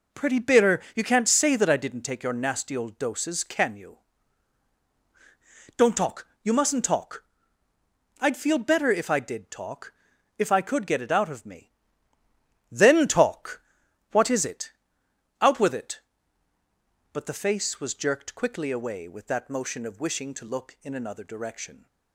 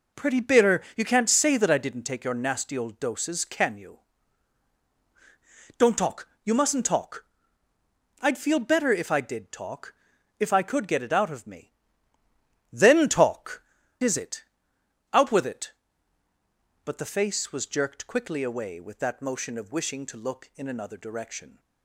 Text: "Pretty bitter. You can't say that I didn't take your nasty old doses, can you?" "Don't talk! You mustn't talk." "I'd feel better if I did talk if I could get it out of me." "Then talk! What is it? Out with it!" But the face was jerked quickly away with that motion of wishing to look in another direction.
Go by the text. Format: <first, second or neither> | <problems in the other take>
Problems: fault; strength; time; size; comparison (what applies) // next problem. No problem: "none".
first | pauses between "talk" and "if"; at 9.9 s; 0.44 s long; also in the first // skips "What"; at 13.8 s